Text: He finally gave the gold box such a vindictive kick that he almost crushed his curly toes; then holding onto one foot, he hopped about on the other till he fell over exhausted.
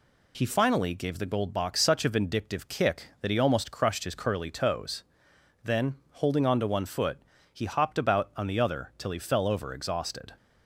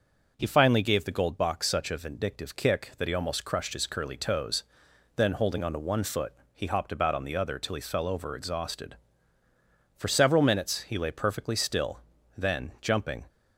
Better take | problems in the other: first | goes on to say "For several minutes he lay perfectly still then jumping"; strong; from 9.9 s on; 3.3 s long

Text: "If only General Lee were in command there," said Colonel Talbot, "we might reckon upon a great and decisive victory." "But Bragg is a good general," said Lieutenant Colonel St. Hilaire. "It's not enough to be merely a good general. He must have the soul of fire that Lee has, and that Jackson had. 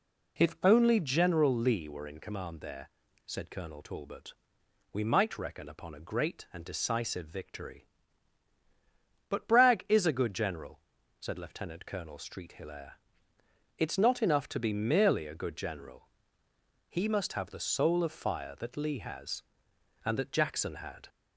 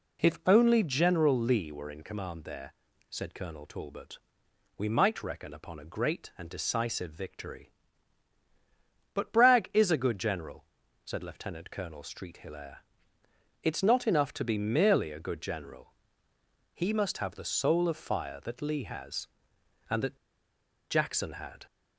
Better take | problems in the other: first | pauses between "that" and "Jackson"; noticeable; at 20.1 s; 0.73 s long

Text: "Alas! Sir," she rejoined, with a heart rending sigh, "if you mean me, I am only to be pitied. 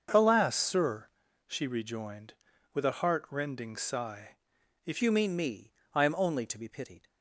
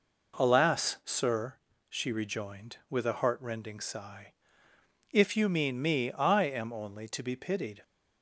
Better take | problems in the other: second | starts louder than the rest; until 1.5 s; 6.5 dB // changes voice at "you"; from 5.0 s on; 2.0 s long

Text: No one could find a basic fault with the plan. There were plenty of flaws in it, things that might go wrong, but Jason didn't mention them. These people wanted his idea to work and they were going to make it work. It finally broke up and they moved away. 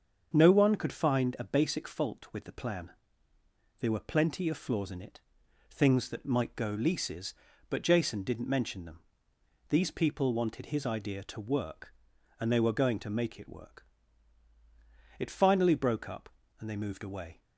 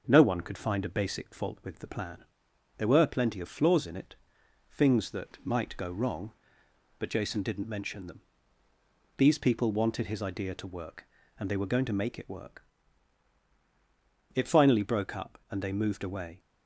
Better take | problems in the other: second | starts louder than the rest; until 1.3 s; 7 dB; also in the second // says "leases" for "wrong"; at 6.7 s

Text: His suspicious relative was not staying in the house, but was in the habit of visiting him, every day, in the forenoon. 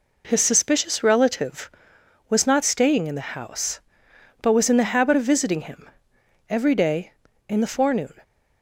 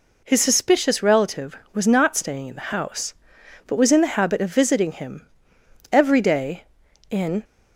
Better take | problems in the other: first | stops before "the forenoon"; at 7.4 s

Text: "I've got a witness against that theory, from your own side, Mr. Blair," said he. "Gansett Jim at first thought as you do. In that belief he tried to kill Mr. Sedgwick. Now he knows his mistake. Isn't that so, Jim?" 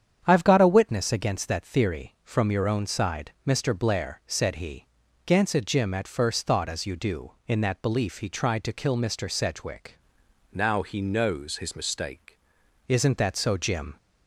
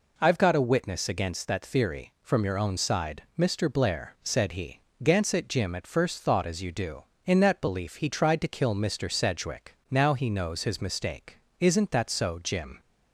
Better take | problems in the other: second | starts louder than the rest; strong; until 1.2 s; 8.5 dB // changes voice from "Now" to "mistake"; from 10.5 to 12.3 s; 1.8 s long

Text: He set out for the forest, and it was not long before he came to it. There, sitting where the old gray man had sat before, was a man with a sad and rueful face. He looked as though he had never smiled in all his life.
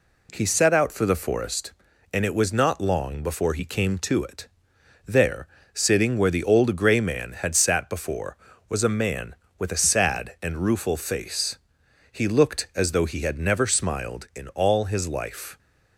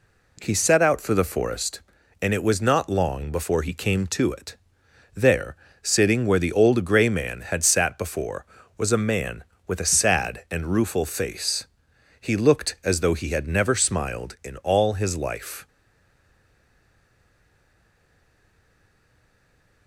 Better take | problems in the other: first | stays silent after the last word; strong; from 15.6 s on; 4.2 s long

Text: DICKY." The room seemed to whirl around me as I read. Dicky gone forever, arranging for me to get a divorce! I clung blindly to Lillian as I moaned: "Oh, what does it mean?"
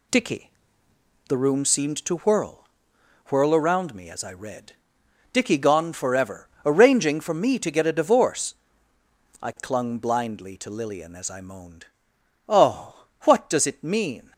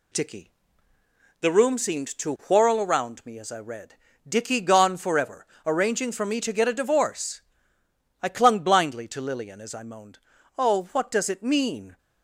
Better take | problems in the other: second | says "whirl" twice; at 3.2 s

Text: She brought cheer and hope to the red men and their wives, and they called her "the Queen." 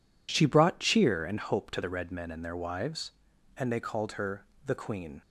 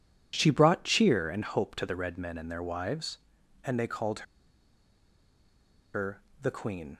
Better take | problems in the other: first | pauses between "called" and "her"; strong; at 4.2 s; 1.6 s long // pauses between "her" and "the"; slight; at 6.2 s; 0.20 s long; slight in the first

